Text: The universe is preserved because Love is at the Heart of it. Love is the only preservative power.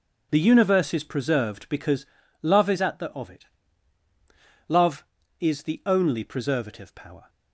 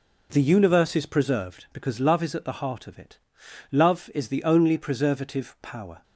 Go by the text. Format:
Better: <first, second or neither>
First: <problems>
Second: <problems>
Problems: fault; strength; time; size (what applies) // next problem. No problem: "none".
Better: second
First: starts louder than the rest; until 1.3 s; 6.5 dB // pauses between "because" and "Love"; slight; at 2.0 s; 0.36 s long // skips "Heart"; at 3.1 s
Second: none